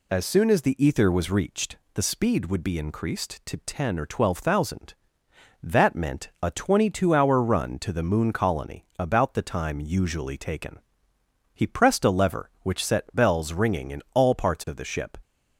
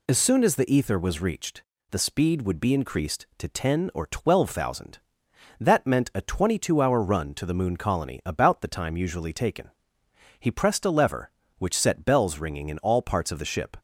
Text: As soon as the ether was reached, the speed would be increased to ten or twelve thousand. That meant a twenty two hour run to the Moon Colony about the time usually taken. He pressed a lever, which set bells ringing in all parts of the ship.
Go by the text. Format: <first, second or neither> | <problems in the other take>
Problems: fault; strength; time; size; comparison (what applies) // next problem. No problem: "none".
neither | none